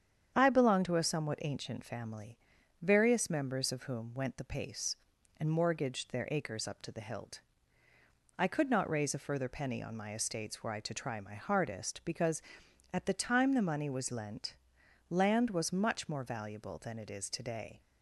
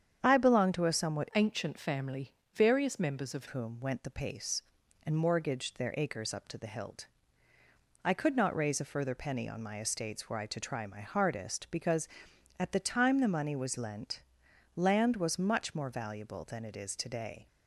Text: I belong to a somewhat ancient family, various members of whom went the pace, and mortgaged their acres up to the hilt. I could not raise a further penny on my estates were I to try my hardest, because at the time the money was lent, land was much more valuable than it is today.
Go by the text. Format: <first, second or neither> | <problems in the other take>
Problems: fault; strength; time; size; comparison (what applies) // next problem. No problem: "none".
first | starts louder than the rest; strong; until 1.2 s; 8 dB; strong in the first // changes voice from "ancient" to "of"; from 1.3 to 3.4 s; 2.1 s long